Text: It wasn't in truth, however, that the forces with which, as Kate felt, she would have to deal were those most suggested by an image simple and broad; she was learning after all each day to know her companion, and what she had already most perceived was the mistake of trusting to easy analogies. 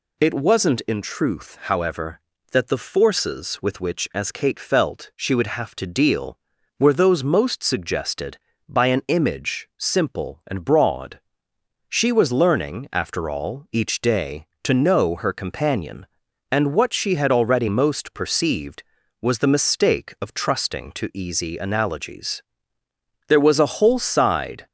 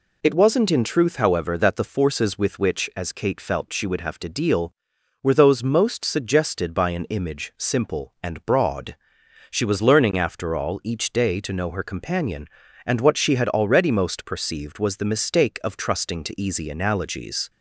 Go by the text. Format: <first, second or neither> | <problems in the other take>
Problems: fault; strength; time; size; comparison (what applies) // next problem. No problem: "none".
second | goes on to say "There was a whole side"; from 23.2 s on; 1.3 s long